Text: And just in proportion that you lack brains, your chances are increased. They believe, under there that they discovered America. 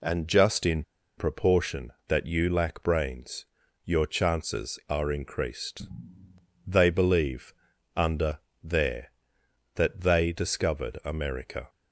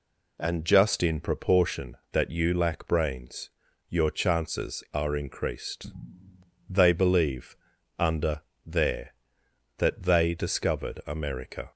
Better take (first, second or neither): second